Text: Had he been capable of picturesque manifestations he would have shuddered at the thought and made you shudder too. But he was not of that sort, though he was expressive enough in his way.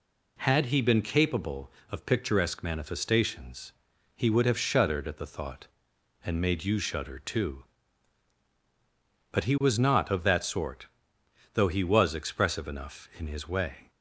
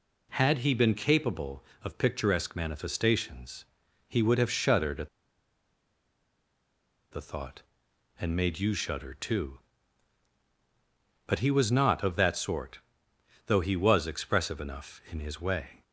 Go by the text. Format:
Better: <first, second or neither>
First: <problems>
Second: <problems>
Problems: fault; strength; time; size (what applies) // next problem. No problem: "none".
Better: first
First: pauses between "manifestations" and "he"; at 3.7 s; 0.44 s long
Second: pauses between "manifestations" and "he"; at 3.6 s; 0.44 s long // pauses between "at" and "the"; strong; at 5.0 s; 2.0 s long